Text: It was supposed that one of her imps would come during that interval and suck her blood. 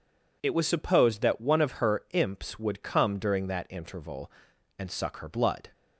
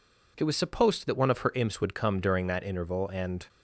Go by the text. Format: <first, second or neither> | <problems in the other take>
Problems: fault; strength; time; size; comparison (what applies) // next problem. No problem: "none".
first | stops before "suck her blood"; at 3.4 s